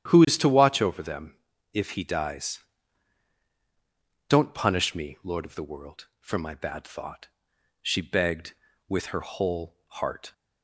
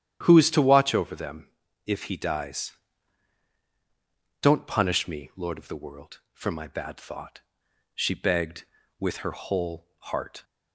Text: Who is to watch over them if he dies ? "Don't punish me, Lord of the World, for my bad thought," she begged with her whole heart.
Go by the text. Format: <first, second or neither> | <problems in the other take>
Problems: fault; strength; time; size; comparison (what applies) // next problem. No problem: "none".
neither | starts louder than the rest; strong; the same in both // pauses between "them" and "if"; the same in both